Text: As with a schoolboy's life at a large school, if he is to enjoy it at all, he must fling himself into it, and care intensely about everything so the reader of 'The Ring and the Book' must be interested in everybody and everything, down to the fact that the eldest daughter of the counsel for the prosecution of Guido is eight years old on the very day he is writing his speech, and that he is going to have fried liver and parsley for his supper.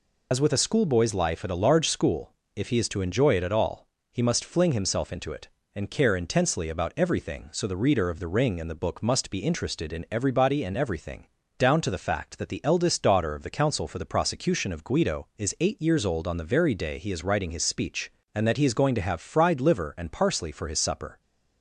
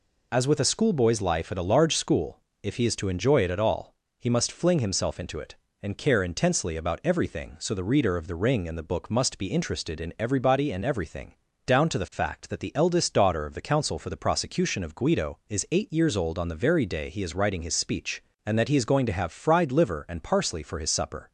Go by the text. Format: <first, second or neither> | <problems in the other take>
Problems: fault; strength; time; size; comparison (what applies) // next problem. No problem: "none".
second | loses the start of "As"; at 0.3 s; 55 ms